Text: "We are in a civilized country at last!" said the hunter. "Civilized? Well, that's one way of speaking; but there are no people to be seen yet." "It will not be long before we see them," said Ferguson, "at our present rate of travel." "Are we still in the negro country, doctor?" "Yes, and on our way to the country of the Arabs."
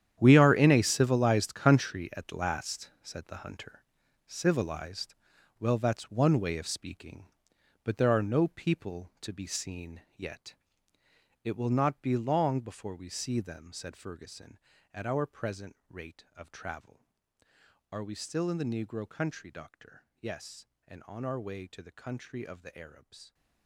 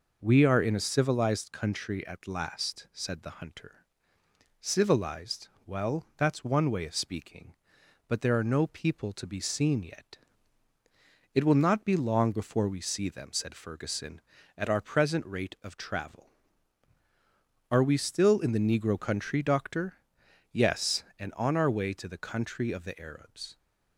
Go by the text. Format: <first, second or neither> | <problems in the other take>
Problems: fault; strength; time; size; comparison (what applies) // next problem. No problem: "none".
second | gets quieter; strong; throughout; 15 dB